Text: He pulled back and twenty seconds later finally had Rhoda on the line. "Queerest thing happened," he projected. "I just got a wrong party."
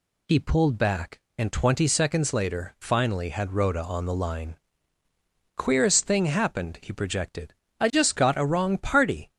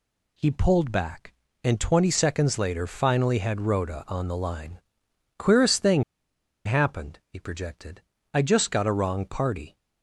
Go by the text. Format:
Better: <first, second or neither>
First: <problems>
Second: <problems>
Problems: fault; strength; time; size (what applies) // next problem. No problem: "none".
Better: first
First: none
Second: pauses between "thing" and "happened"; noticeable; at 6.0 s; 0.63 s long